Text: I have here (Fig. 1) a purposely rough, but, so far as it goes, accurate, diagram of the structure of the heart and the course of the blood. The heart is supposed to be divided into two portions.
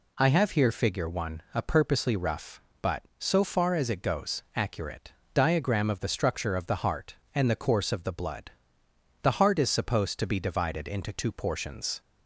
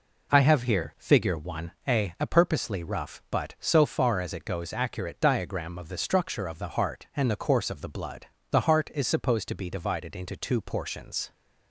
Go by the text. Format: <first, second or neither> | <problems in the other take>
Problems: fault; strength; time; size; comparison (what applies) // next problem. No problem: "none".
first | says "a" twice; at 2.2 s